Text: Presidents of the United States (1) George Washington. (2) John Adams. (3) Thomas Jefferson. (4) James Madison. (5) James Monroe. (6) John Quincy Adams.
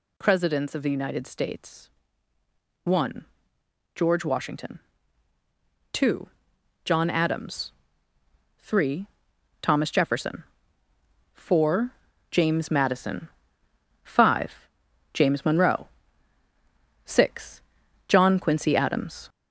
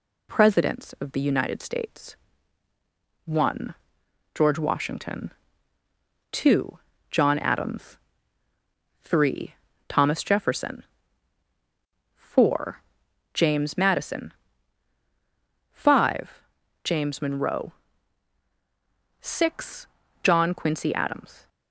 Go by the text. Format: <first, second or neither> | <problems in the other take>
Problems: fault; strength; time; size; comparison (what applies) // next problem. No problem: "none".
second | gets louder; throughout; 3.5 dB